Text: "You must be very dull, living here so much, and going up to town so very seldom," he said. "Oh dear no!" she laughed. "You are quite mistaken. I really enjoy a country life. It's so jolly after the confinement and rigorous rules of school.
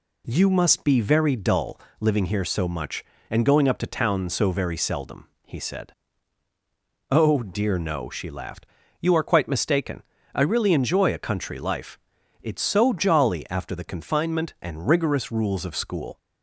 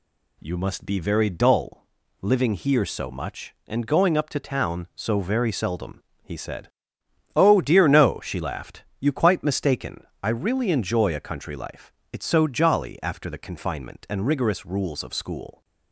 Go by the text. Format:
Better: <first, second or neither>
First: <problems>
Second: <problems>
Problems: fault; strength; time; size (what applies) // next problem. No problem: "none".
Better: first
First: none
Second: skips "are"; at 9.1 s